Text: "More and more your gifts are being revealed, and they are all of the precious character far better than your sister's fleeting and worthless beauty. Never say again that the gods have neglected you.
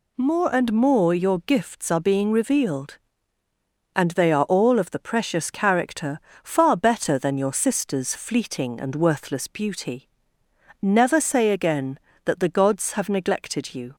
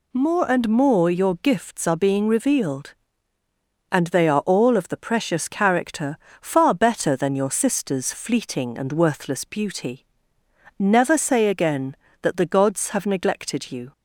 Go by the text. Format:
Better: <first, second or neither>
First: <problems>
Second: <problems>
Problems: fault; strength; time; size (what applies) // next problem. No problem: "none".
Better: neither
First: pauses between "character" and "far"; slight; at 6.1 s; 0.24 s long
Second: pauses between "character" and "far"; slight; at 6.1 s; 0.24 s long